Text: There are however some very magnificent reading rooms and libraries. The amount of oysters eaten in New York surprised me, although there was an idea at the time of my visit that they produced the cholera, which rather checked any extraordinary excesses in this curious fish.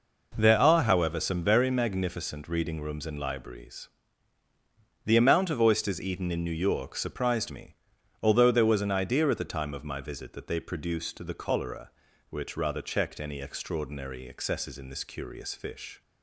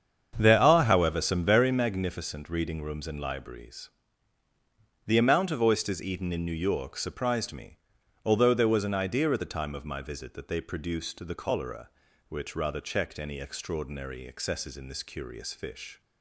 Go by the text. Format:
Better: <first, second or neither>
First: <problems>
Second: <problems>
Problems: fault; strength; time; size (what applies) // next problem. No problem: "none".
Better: first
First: none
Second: starts louder than the rest; strong; until 2.0 s; 7.5 dB